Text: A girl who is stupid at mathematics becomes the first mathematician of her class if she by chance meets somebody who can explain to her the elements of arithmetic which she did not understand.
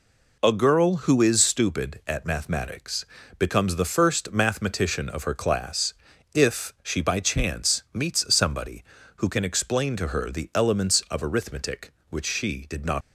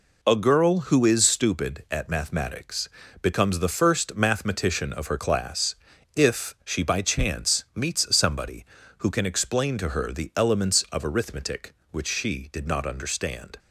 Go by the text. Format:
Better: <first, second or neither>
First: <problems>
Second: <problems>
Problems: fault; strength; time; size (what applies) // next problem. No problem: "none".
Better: second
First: pauses between "mathematics" and "becomes"; slight; at 3.0 s; 0.36 s long // pauses between "class" and "if"; at 5.9 s; 0.38 s long // stops before "understand"; at 13.0 s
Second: pauses between "mathematics" and "becomes"; slight; at 2.8 s; 0.36 s long // pauses between "class" and "if"; at 5.7 s; 0.38 s long